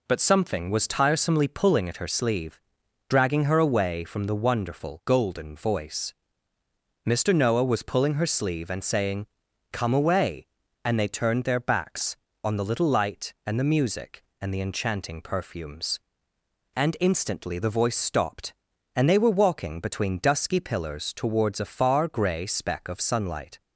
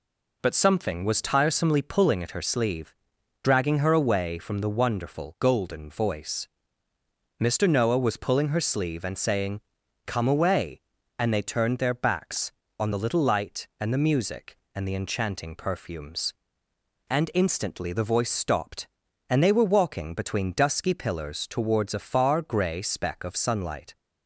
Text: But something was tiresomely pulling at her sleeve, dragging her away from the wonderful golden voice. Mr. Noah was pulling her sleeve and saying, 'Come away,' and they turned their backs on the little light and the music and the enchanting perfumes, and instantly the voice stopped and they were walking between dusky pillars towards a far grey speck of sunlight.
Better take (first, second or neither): neither